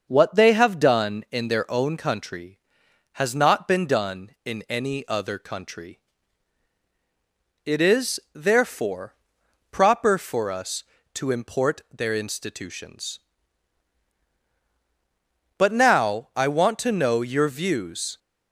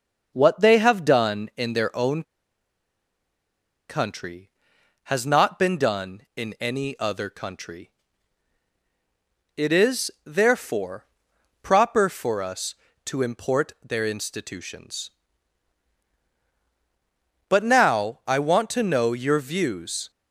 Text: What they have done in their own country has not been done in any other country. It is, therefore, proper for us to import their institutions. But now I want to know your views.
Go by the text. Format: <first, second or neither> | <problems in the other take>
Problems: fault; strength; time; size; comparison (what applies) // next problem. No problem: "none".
first | starts louder than the rest; until 1.3 s; 6 dB; also in the first // pauses between "own" and "country"; strong; at 2.2 s; 1.6 s long